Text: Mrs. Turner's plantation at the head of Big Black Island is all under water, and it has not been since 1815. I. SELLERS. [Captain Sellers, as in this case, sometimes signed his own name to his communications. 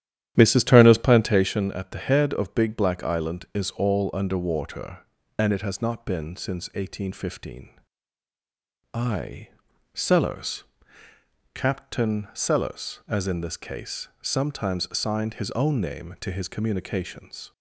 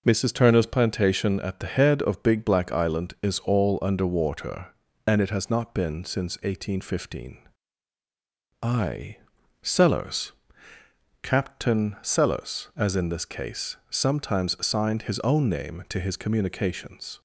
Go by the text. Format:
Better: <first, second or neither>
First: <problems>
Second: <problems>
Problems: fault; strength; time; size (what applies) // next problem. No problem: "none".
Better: second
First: starts louder than the rest; strong; until 1.5 s; 11 dB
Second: none